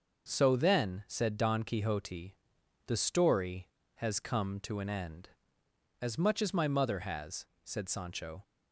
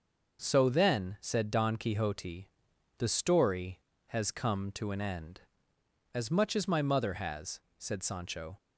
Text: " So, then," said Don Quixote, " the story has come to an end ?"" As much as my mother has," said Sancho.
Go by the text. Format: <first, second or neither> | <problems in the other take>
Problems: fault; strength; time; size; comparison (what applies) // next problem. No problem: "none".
neither | starts louder than the rest; the same in both